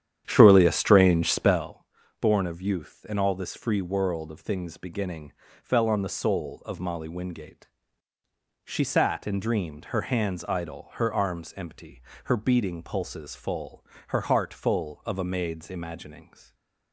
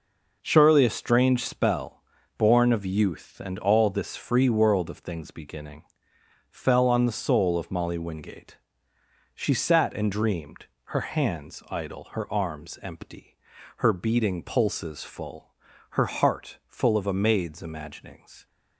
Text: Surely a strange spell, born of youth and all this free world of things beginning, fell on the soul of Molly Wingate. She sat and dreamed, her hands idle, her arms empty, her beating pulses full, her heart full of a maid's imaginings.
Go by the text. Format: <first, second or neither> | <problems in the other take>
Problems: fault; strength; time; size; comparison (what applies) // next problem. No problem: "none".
second | starts louder than the rest; strong; until 1.7 s; 10 dB // stays silent after the last word; slight; from 16.2 s on; 0.7 s long